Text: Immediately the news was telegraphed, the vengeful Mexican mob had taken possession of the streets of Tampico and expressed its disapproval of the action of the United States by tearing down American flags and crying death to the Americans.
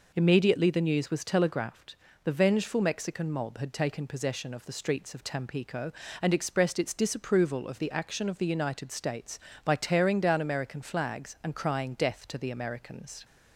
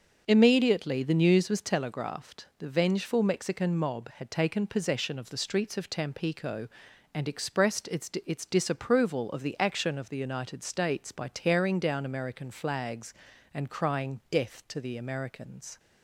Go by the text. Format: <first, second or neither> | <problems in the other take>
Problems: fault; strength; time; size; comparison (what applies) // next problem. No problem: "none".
first | says "its" twice; at 8.2 s